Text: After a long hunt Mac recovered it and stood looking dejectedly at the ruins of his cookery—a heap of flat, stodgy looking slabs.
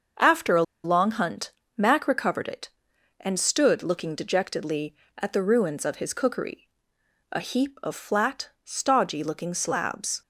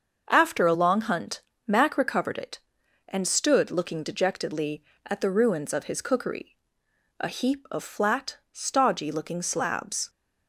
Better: second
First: starts louder than the rest; until 1.4 s; 6.5 dB // pauses between "a" and "long"; slight; at 0.6 s; 0.21 s long // pauses between "hunt" and "Mac"; slight; at 1.5 s; 0.24 s long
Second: starts louder than the rest; until 1.3 s; 6.5 dB // pauses between "hunt" and "Mac"; slight; at 1.4 s; 0.24 s long

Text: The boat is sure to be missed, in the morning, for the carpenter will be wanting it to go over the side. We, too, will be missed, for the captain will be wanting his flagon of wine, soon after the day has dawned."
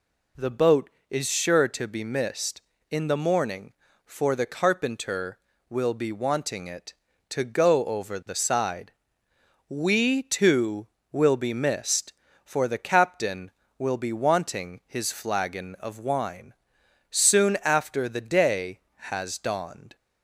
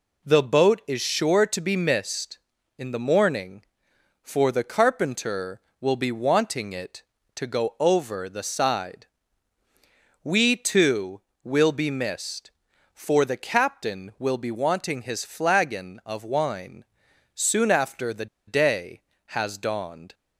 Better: first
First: none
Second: pauses between "the" and "day"; slight; at 18.2 s; 0.20 s long

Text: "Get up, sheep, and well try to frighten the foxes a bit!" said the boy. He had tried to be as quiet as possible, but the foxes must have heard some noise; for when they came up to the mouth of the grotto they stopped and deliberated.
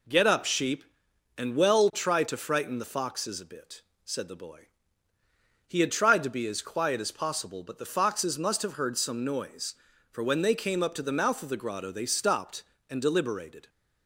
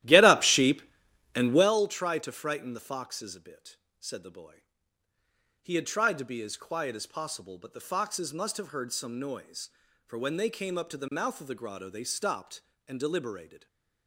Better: first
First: none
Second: starts louder than the rest; strong; until 1.7 s; 14 dB

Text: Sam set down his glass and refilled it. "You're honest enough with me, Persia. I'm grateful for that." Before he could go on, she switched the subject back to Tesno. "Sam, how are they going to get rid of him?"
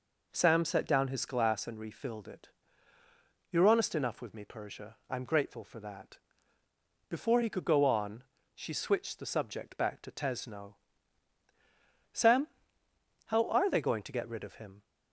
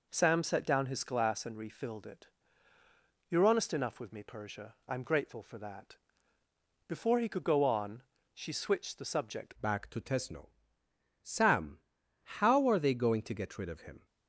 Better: first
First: none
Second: changes voice at "back"; from 9.6 s on; 4.4 s long

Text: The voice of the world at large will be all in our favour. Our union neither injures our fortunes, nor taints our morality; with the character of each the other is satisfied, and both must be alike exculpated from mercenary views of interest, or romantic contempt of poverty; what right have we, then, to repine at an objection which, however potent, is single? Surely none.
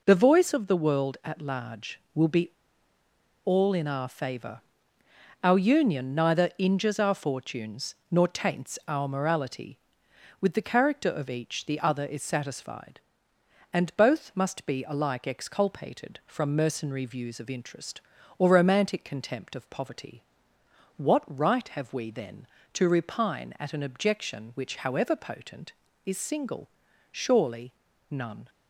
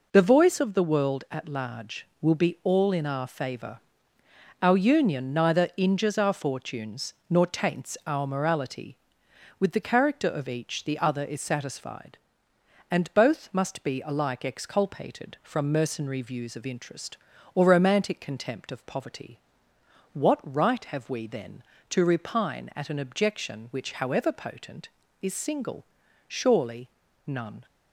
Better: second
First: pauses between "be" and "all"; noticeable; at 2.5 s; 0.94 s long // pauses between "Surely" and "none"; at 27.7 s; 0.38 s long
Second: pauses between "Surely" and "none"; at 26.8 s; 0.38 s long

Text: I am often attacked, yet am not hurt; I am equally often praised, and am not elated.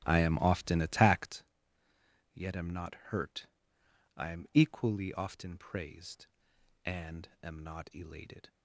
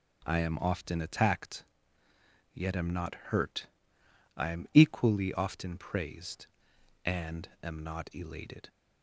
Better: second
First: starts louder than the rest; strong; until 1.4 s; 13.5 dB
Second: none

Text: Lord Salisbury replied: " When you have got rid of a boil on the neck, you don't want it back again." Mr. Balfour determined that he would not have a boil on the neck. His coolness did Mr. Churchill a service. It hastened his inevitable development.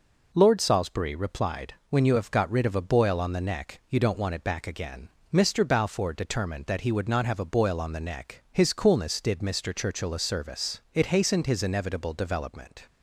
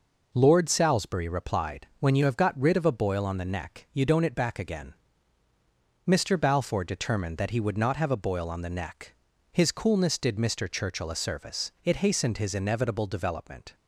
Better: first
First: none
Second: skips "want"; at 4.2 s

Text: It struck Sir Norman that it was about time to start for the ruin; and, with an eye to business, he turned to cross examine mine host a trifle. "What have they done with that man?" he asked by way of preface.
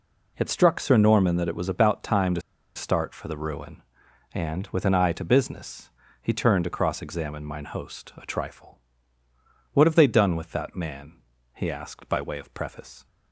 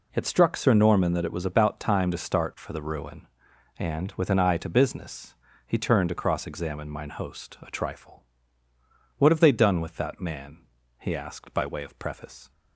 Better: second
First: pauses between "to" and "start"; slight; at 2.3 s; 0.35 s long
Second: none

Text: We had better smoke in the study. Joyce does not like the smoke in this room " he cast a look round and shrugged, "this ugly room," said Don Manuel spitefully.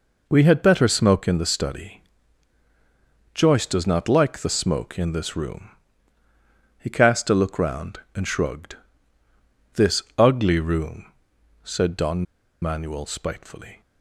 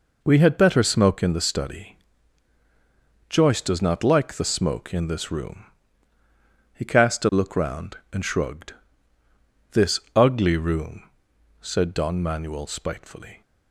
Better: second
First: pauses between "this" and "ugly"; slight; at 10.0 s; 0.16 s long // pauses between "Don" and "Manuel"; at 12.2 s; 0.37 s long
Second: pauses between "this" and "ugly"; slight; at 9.9 s; 0.16 s long

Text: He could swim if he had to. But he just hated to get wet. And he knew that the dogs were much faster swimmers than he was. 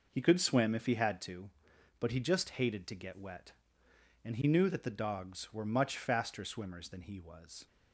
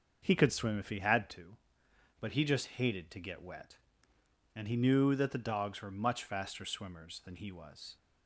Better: neither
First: none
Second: none

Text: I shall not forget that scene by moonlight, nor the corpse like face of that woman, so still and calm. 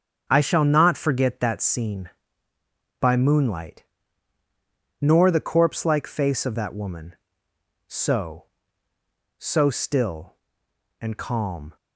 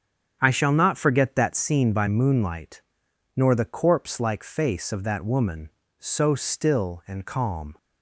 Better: second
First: starts louder than the rest; strong; until 1.3 s; 7 dB // says "so" twice; at 9.3 s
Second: starts louder than the rest; strong; until 1.4 s; 8 dB

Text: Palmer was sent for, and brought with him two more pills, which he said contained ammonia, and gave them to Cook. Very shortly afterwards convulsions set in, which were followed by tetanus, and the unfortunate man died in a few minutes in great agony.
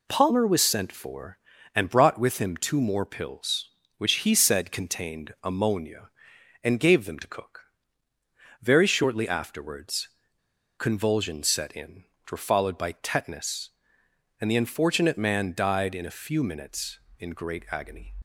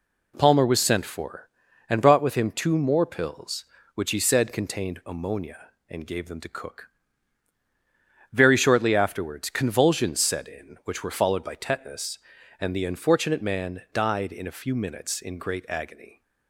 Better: second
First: pauses between "afterwards" and "convulsions"; noticeable; at 10.0 s; 0.70 s long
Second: none

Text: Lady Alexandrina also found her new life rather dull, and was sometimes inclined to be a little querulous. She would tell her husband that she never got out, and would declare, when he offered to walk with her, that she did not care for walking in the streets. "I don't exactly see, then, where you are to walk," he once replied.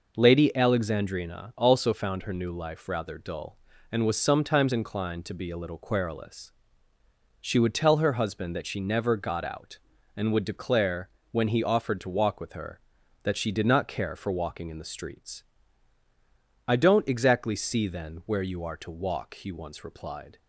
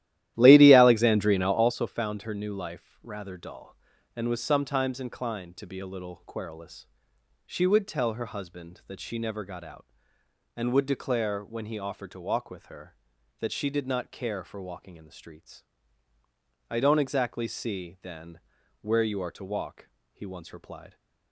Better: first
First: none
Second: starts louder than the rest; strong; until 1.7 s; 13.5 dB

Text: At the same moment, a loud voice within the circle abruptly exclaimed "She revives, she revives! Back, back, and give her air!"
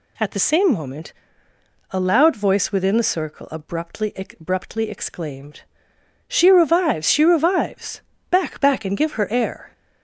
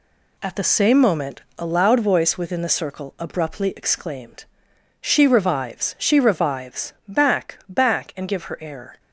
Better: second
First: says "abruptly" twice; at 4.1 s // pauses between "exclaimed" and "She"; noticeable; at 5.6 s; 0.66 s long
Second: pauses between "exclaimed" and "She"; noticeable; at 4.4 s; 0.56 s long

